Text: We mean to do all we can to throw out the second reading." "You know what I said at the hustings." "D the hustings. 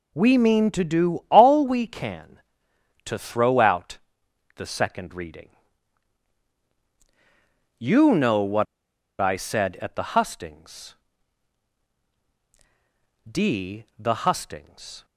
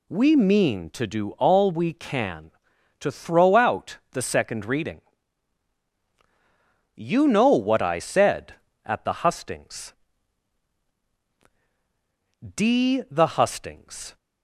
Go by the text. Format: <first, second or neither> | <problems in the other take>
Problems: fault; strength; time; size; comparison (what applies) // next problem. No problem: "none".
second | pauses between "out" and "the"; noticeable; at 3.9 s; 0.60 s long // pauses between "what" and "I"; noticeable; at 8.6 s; 0.55 s long